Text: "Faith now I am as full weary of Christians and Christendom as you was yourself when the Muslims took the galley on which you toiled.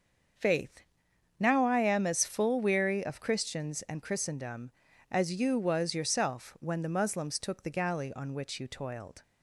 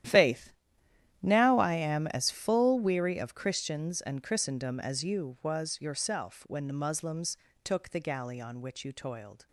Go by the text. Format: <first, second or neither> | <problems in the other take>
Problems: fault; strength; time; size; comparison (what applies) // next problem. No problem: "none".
first | gets quieter; strong; throughout; 15.5 dB // starts louder than the rest; strong; until 1.7 s; 11.5 dB; also in the first // pauses between "Faith" and "now"; noticeable; at 0.5 s; 0.68 s long; noticeable in the first // pauses between "Muslims" and "took"; slight; at 7.3 s; 0.26 s long